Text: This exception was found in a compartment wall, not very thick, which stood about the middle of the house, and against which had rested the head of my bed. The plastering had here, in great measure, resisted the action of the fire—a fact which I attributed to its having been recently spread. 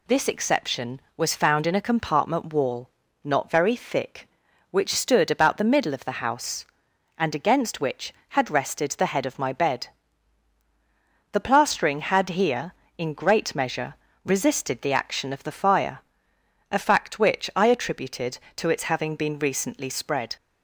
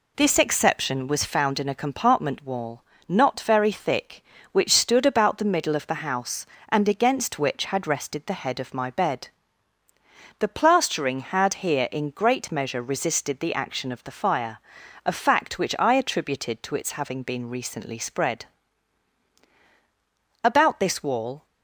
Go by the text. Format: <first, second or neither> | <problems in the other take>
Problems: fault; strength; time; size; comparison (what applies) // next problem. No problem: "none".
first | goes on to say "About this wall"; noticeable; from 20.4 s on; 1.0 s long